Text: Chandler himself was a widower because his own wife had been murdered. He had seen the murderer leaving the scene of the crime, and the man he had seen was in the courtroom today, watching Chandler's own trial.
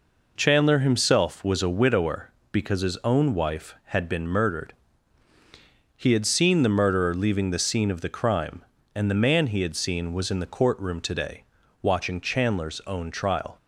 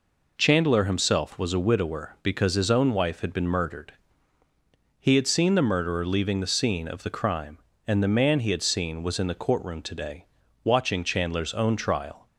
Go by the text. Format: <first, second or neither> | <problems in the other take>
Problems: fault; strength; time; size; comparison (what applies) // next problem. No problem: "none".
neither | none